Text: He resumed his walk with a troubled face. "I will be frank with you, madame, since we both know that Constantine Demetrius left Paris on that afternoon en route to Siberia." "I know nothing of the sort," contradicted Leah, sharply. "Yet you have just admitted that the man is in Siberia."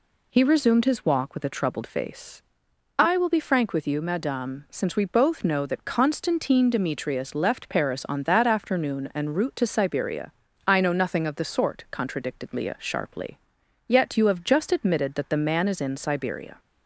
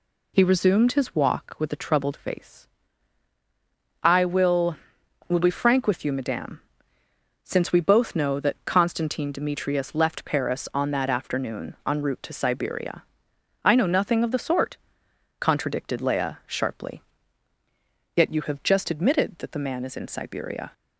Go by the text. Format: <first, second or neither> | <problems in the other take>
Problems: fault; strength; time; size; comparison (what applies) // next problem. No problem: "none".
first | says "will" twice; at 5.2 s